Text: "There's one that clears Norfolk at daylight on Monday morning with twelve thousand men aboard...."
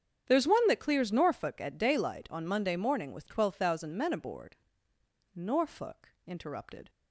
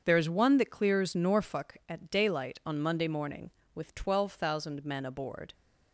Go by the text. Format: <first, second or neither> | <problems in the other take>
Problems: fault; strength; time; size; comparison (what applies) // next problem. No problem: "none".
second | starts louder than the rest; strong; until 1.3 s; 8 dB; also in the second // goes on to say "Norfolk interrupted"; from 5.3 s on; 1.5 s long